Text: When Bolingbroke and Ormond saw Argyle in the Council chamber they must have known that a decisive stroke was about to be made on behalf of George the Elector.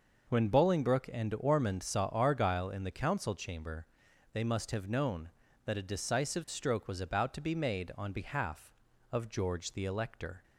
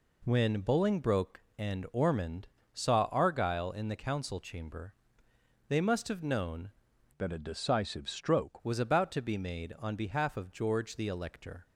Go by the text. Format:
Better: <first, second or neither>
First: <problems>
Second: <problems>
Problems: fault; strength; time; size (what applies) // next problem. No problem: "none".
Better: first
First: pauses between "chamber" and "they"; noticeable; at 3.8 s; 0.48 s long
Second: pauses between "Ormond" and "saw"; slight; at 2.4 s; 0.26 s long // pauses between "chamber" and "they"; noticeable; at 4.9 s; 0.74 s long // changes voice from "that" to "stroke"; from 7.1 to 8.6 s; 1.5 s long